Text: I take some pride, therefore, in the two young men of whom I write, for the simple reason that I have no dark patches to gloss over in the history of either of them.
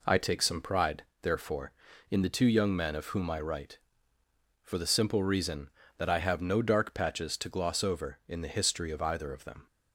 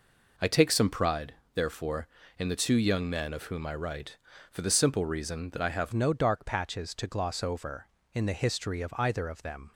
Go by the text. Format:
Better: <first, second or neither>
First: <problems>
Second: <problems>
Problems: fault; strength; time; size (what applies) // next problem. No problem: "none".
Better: first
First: none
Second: changes voice at "no"; from 5.9 s on; 3.8 s long